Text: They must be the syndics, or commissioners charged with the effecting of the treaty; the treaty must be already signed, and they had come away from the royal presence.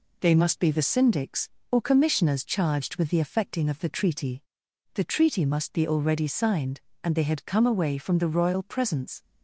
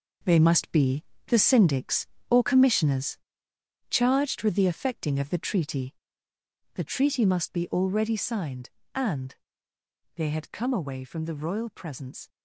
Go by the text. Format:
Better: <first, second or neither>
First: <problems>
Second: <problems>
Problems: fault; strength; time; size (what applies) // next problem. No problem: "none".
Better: first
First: none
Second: gets quieter; strong; throughout; 9.5 dB // pauses between "be" and "the"; slight; at 1.0 s; 0.24 s long // pauses between "commissioners" and "charged"; noticeable; at 3.1 s; 0.74 s long // pauses between "and" and "they"; noticeable; at 9.3 s; 0.80 s long